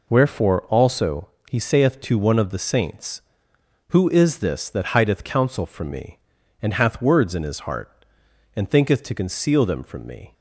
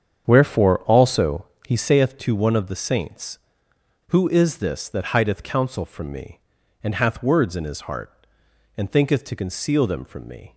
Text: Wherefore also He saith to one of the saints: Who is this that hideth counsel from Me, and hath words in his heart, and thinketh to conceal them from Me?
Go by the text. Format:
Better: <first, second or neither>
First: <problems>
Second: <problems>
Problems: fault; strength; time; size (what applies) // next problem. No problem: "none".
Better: first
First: pauses between "also" and "He"; slight; at 1.2 s; 0.20 s long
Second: starts louder than the rest; strong; until 2.1 s; 8 dB // pauses between "also" and "He"; slight; at 1.4 s; 0.20 s long